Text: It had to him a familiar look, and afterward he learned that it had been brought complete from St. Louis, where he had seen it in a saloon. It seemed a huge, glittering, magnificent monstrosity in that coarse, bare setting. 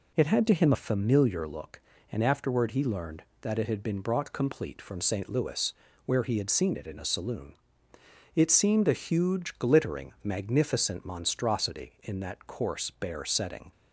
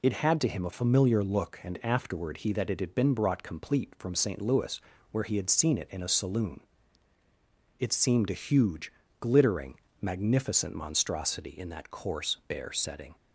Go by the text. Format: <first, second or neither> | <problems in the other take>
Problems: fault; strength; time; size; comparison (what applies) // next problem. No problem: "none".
first | skips "learned"; at 2.5 s